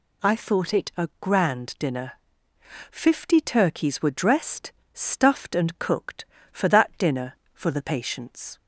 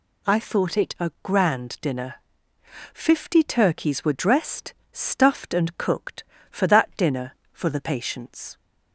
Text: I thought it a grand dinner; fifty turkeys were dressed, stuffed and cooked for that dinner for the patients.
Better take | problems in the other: neither | none

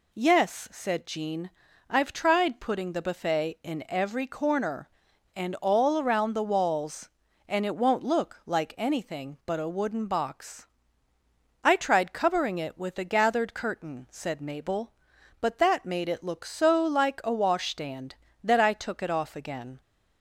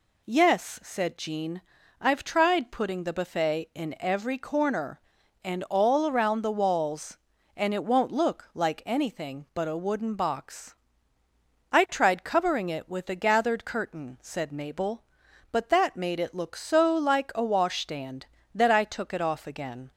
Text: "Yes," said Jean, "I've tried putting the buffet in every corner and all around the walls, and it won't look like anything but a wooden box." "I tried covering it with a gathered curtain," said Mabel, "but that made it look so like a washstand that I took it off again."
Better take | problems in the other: neither | none

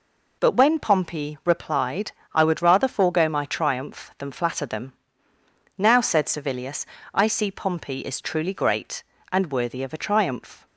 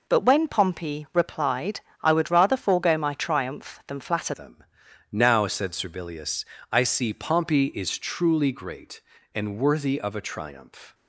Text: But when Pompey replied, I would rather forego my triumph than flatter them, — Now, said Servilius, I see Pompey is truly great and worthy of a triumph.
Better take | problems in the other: first | changes voice at "them"; from 4.3 s on; 6.6 s long

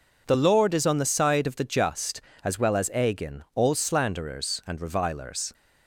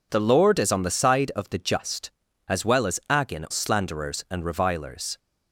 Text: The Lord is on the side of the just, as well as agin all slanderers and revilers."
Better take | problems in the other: first | skips "all"; at 3.4 s

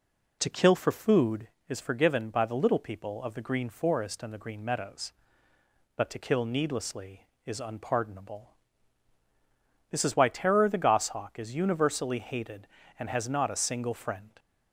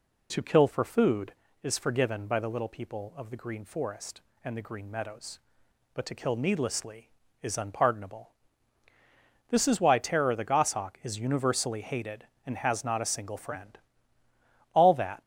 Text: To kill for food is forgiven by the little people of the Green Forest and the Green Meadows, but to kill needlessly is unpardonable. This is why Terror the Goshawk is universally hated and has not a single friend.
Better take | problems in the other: first | goes on to say "All that"; slight; from 14.7 s on; 0.48 s long

